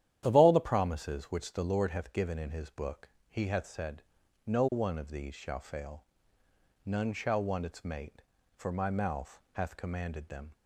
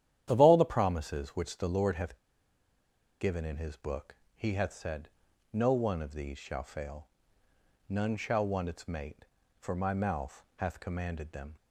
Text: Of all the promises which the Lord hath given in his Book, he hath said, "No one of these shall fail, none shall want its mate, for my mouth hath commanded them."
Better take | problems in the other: first | starts louder than the rest; strong; until 1.2 s; 11 dB; strong in the first // pauses between "hath" and "given"; at 2.1 s; 1.0 s long

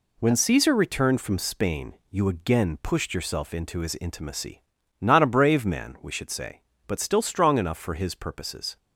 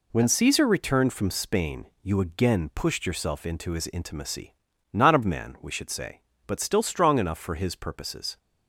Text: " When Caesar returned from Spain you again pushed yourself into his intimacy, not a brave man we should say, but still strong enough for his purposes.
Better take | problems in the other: first | pauses between "Spain" and "you"; slight; at 1.8 s; 0.16 s long; slight in the first // skips "brave"; at 5.2 s

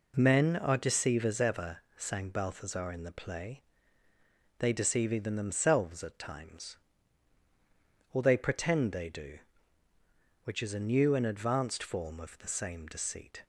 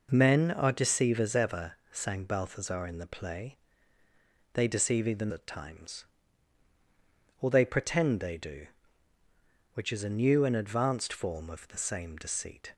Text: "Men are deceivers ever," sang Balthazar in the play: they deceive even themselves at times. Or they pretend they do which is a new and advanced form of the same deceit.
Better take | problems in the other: first | skips "themselves"; at 5.3 s

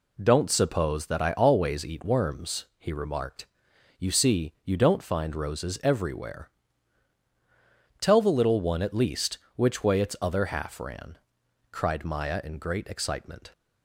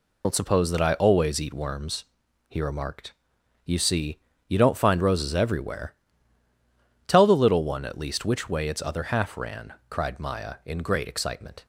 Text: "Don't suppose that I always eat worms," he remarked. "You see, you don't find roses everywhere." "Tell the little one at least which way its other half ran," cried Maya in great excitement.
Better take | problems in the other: first | loses the start of "Don't"; at 0.2 s; 95 ms

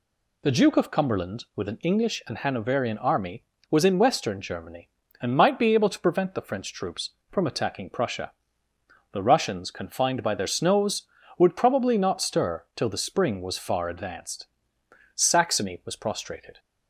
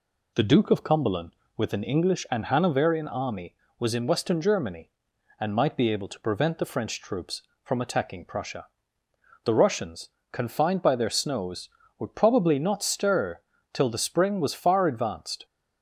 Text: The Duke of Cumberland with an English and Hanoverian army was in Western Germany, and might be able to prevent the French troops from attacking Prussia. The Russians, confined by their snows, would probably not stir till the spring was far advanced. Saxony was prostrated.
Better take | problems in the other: first | pauses between "stir" and "till"; slight; at 13.4 s; 0.32 s long // stops before "Saxony was prostrated"; at 15.4 s

